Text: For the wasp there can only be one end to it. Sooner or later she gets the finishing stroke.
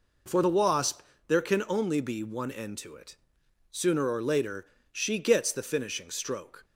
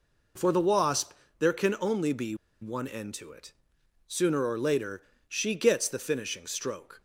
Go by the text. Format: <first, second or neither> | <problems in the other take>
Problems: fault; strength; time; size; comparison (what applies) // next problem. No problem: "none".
first | pauses between "wasp" and "there"; slight; at 1.1 s; 0.26 s long; slight in the first // pauses between "be" and "one"; slight; at 2.3 s; 0.27 s long // pauses between "later" and "she"; slight; at 5.0 s; 0.24 s long; slight in the first